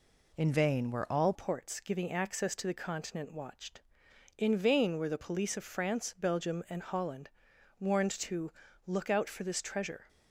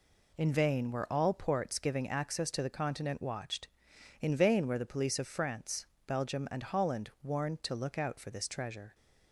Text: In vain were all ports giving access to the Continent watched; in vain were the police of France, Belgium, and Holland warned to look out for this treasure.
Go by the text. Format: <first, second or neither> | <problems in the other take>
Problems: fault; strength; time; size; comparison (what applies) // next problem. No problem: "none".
second | changes voice at "ports"; from 1.3 s on; 8.7 s long // pauses between "Holland" and "warned"; noticeable; at 7.2 s; 0.50 s long // pauses between "to" and "look"; slight; at 8.5 s; 0.34 s long